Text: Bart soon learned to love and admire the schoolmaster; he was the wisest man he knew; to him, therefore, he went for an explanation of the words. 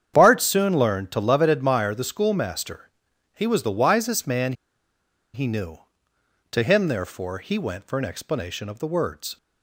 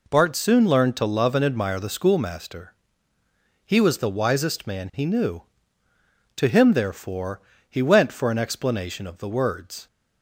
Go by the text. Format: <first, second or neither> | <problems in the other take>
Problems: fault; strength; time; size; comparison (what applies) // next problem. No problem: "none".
second | starts louder than the rest; strong; until 1.1 s; 8.5 dB // pauses between "man" and "he"; noticeable; at 4.5 s; 0.81 s long